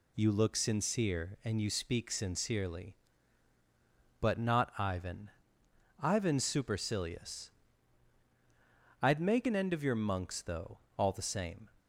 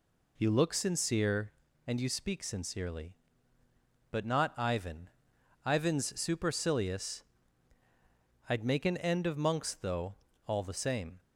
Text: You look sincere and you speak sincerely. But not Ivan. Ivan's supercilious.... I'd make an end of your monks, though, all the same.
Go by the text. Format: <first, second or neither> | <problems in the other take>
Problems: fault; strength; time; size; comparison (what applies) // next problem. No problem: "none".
first | skips "your"; at 9.3 s